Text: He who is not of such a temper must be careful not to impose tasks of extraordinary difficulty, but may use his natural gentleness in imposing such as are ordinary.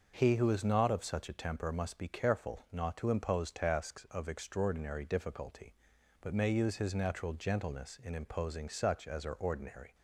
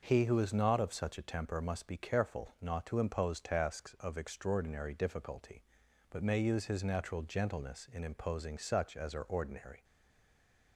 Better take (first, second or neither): first